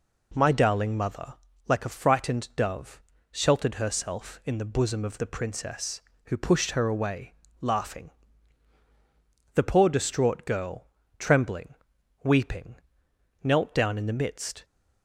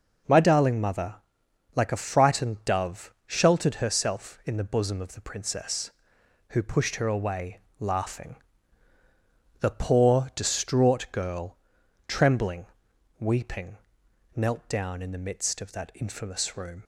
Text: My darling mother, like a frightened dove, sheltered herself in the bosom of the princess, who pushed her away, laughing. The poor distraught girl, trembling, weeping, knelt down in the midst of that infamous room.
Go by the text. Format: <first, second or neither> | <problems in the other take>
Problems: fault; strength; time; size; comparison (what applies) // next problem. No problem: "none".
second | stops before "of that infamous room"; at 14.6 s